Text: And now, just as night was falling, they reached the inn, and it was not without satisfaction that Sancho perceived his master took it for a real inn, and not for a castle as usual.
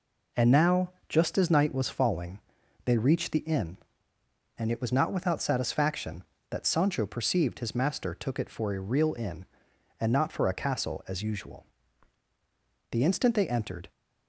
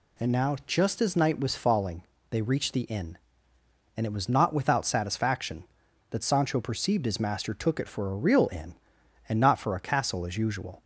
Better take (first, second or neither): second